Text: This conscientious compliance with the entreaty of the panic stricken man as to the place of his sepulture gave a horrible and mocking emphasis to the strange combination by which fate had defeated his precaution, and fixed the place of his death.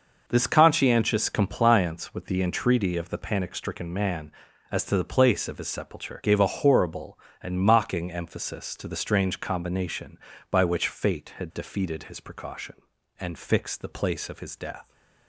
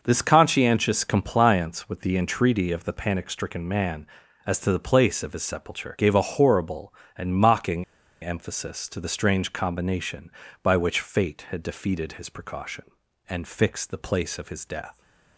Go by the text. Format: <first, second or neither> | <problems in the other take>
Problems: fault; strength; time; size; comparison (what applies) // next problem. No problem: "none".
first | pauses between "mocking" and "emphasis"; at 7.8 s; 0.38 s long